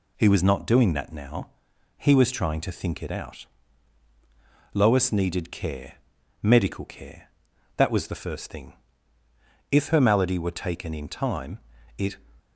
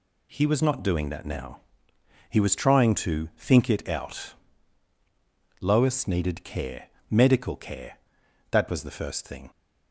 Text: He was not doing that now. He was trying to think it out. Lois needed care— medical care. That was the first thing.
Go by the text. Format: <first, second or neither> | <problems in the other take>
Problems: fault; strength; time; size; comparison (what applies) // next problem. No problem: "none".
second | goes on to say "If her malady were taken in time it"; strong; from 9.7 s on; 2.4 s long